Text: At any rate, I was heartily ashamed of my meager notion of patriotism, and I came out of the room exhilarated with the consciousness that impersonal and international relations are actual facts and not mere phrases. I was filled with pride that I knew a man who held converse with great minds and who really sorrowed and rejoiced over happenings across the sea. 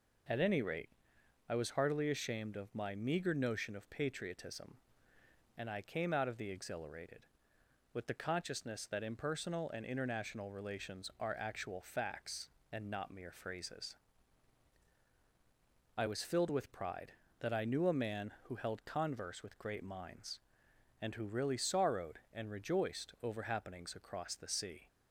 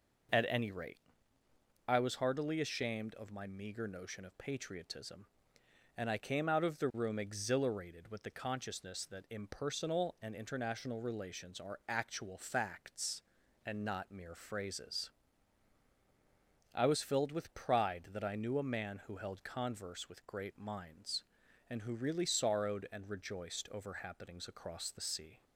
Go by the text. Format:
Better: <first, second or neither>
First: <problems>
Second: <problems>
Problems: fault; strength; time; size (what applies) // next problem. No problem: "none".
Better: second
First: skips "room"; at 6.5 s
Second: none